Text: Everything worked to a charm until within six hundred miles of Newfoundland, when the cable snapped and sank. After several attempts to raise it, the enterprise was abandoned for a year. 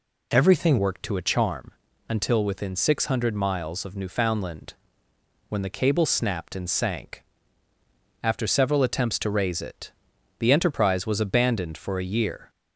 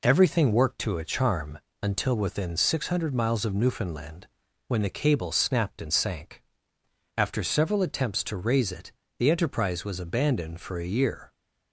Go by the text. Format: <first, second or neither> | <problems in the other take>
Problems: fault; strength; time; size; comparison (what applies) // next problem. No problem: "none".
second | changes voice at "worked"; from 0.7 s on; 11.7 s long // pauses between "charm" and "until"; at 1.6 s; 0.38 s long; slight in the second